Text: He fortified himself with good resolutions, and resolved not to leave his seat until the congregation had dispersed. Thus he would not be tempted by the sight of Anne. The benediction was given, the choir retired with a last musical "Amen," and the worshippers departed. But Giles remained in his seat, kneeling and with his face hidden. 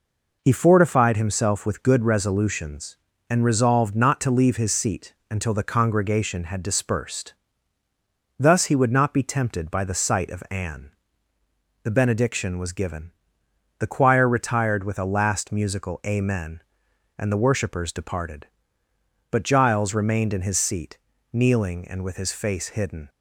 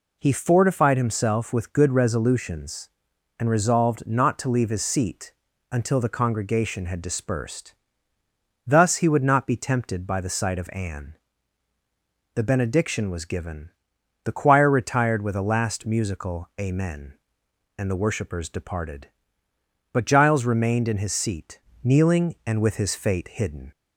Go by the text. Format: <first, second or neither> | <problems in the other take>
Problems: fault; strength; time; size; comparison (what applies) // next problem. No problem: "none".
first | pauses between "seat" and "until"; at 5.3 s; 0.40 s long; slight in the first // says "fate" for "face"; at 22.9 s